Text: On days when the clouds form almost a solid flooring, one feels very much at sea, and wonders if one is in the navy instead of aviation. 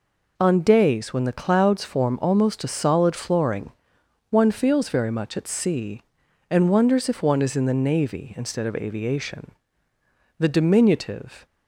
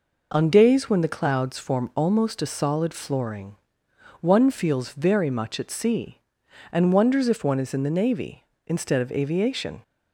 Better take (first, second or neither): second